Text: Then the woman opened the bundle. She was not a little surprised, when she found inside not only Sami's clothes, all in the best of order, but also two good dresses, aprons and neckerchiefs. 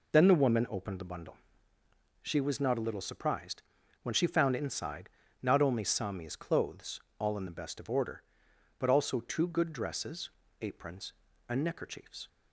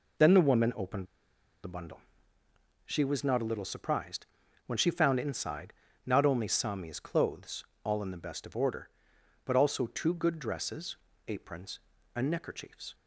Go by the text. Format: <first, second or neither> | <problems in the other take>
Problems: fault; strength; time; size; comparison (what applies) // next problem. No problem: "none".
first | pauses between "opened" and "the"; noticeable; at 1.0 s; 0.59 s long // pauses between "inside" and "not"; slight; at 5.7 s; 0.34 s long; slight in the first